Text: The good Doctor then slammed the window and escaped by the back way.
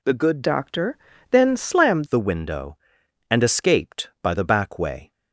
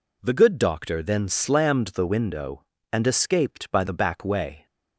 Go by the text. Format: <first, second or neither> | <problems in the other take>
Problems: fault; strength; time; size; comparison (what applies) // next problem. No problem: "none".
second | changes voice from "Doctor" to "slammed"; from 0.4 to 2.0 s; 1.6 s long // pauses between "Doctor" and "then"; slight; at 0.9 s; 0.32 s long